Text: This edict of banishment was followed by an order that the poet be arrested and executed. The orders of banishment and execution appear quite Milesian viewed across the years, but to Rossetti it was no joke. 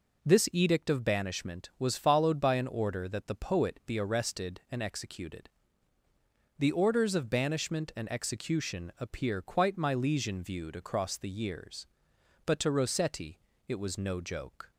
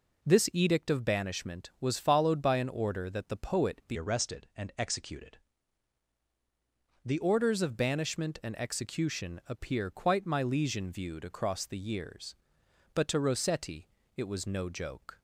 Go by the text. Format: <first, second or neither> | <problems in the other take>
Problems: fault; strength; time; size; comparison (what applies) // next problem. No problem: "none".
first | changes voice from "arrested" to "The"; from 3.9 to 7.1 s; 3.2 s long // pauses between "Rossetti" and "it"; slight; at 13.8 s; 0.30 s long; slight in the first